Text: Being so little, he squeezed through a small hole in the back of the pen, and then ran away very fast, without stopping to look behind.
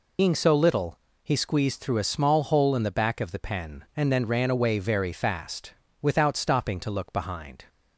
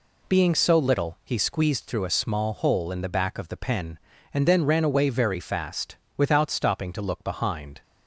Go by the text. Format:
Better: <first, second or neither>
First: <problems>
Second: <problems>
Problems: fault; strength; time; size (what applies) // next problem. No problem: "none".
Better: second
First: loses the start of "Being"; at 0.1 s; 90 ms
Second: none